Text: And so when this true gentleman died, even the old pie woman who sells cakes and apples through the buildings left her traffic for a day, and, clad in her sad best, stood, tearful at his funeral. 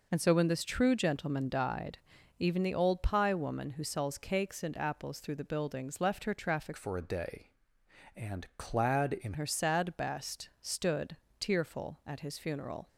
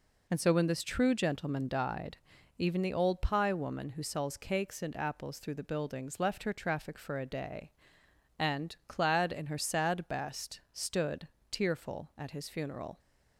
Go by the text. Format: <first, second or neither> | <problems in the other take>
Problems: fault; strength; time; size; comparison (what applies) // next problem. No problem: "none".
second | changes voice from "for" to "in"; from 6.7 to 9.3 s; 2.6 s long